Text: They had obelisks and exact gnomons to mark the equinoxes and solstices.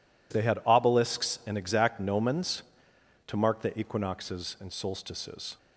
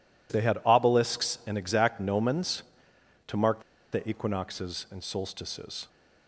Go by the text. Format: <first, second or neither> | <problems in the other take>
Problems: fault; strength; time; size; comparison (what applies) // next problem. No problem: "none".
first | pauses between "mark" and "the"; slight; at 3.6 s; 0.29 s long